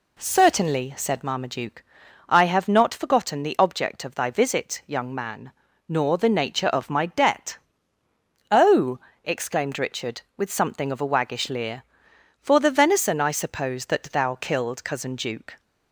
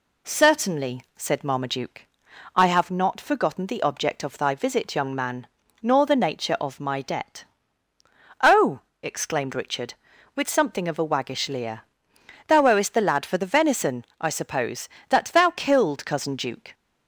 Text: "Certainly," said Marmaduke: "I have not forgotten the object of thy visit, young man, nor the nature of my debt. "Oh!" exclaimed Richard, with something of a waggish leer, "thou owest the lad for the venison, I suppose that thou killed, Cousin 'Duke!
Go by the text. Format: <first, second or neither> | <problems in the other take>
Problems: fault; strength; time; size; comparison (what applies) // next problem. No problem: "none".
second | skips "thou owest the lad"; at 12.1 s